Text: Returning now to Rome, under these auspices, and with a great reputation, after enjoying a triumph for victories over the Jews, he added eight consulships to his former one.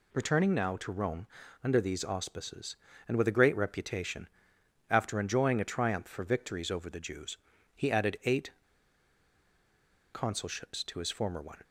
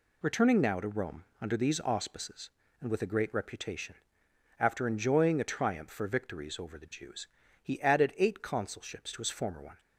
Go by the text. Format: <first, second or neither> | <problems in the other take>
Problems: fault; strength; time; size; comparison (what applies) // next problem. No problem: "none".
second | pauses between "eight" and "consulships"; strong; at 8.5 s; 1.6 s long